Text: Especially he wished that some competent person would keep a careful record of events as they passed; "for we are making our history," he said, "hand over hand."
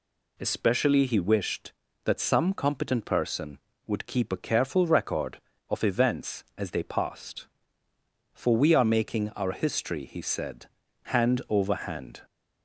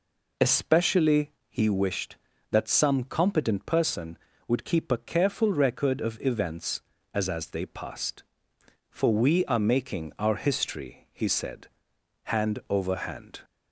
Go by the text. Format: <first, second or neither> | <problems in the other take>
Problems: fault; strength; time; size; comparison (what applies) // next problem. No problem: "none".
first | pauses between "Especially" and "he"; slight; at 1.3 s; 0.18 s long // says "as" twice; at 7.2 s